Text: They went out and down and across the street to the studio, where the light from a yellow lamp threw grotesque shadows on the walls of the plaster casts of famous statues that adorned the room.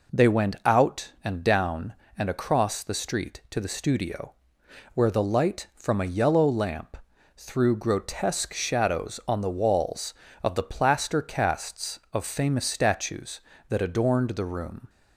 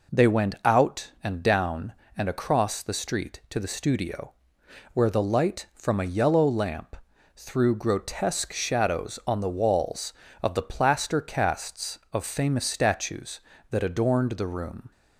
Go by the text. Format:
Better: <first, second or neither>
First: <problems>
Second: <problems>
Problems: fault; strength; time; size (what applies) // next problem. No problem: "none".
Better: neither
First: pauses between "lamp" and "threw"; at 6.9 s; 0.40 s long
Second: pauses between "lamp" and "threw"; at 6.9 s; 0.40 s long